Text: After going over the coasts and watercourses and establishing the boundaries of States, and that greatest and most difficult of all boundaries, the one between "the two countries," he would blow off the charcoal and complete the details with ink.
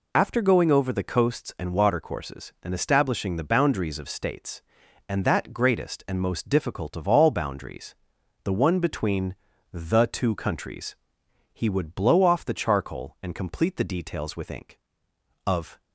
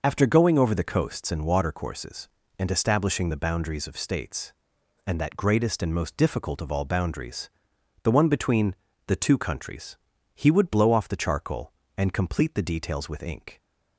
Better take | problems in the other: second | pauses between "between" and "the"; at 9.3 s; 0.38 s long; slight in the second // goes on to say "Of"; slight; from 15.4 s on; 0.32 s long

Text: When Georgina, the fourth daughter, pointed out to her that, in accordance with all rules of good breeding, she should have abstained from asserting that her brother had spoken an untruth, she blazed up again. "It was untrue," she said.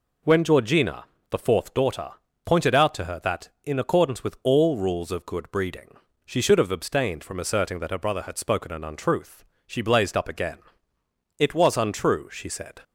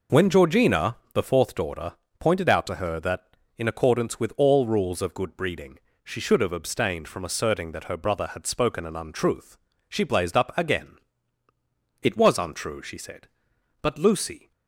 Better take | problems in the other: first | goes on to say "But Lucy"; noticeable; from 13.8 s on; 0.70 s long

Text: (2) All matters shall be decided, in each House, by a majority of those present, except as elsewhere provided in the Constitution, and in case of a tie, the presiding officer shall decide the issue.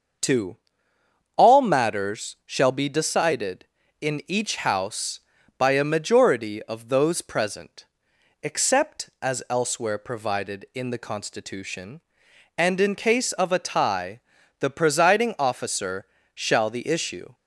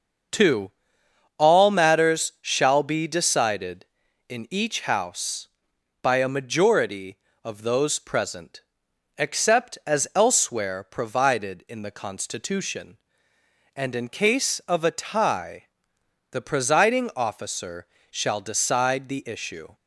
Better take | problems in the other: second | starts louder than the rest; until 2.0 s; 6.5 dB; also in the second // pauses between "officer" and "shall"; slight; at 16.0 s; 0.28 s long; slight in the second // skips "decide"; at 16.7 s

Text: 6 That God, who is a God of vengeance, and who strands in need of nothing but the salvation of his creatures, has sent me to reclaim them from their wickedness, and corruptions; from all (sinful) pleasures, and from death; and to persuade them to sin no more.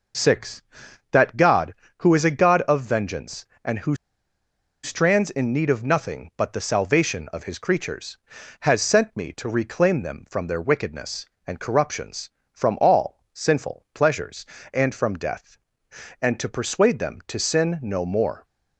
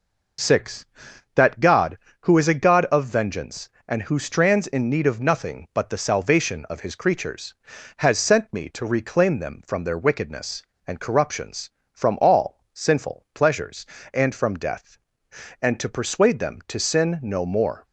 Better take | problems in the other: second | pauses between "who" and "strands"; noticeable; at 3.9 s; 0.89 s long

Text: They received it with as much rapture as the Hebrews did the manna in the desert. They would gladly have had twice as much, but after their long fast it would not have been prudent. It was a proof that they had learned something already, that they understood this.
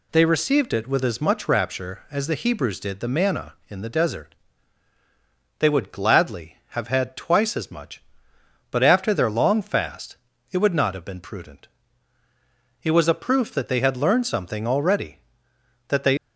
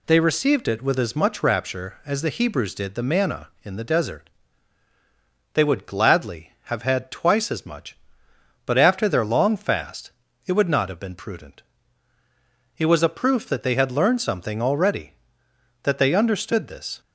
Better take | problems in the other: second | pauses between "fast" and "it"; slight; at 10.1 s; 0.36 s long; slight in the second // stops before "understood this"; at 16.1 s

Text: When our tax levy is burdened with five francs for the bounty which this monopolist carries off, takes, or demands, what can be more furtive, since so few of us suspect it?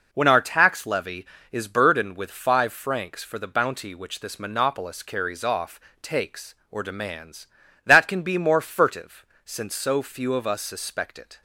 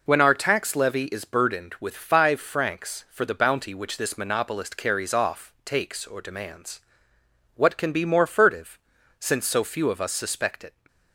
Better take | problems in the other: second | says "that" for "what"; at 7.8 s

